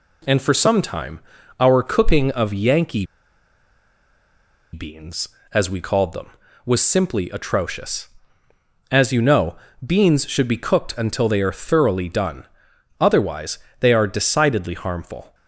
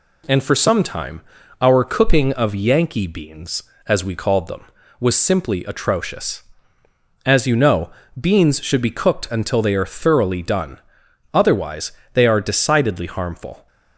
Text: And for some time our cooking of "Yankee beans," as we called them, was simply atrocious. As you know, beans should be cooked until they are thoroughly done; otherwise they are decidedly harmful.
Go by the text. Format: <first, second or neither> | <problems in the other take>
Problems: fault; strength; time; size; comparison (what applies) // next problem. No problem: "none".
second | pauses between "time" and "our"; at 1.1 s; 0.40 s long; also in the second // pauses between "Yankee" and "beans"; strong; at 3.0 s; 1.6 s long // pauses between "otherwise" and "they"; slight; at 13.5 s; 0.22 s long; slight in the second